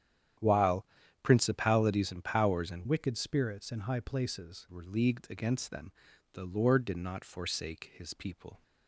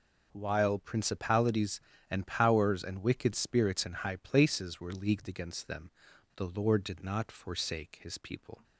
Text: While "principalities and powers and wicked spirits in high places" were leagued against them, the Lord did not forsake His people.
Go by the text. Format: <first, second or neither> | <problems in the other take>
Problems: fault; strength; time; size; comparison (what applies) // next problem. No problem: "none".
second | starts louder than the rest; strong; until 1.7 s; 10 dB // pauses between "While" and "principalities"; at 0.8 s; 0.38 s long // changes voice from "wicked" to "places"; from 2.8 to 4.6 s; 1.8 s long